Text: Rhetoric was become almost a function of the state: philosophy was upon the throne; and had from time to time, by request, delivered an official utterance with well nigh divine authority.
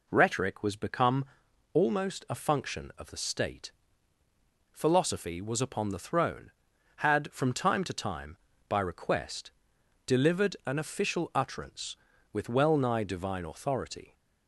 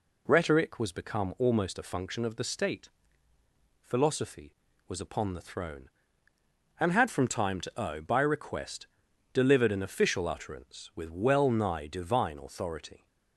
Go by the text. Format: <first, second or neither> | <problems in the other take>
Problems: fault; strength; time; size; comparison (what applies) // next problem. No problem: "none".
second | pauses between "become" and "almost"; noticeable; at 1.2 s; 0.48 s long // skips "and"; at 6.7 s